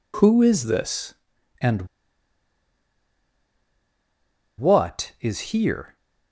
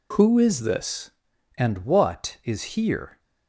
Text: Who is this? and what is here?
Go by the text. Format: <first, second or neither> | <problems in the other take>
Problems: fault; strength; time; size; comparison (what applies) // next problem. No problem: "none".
second | pauses between "and" and "what"; strong; at 1.8 s; 2.7 s long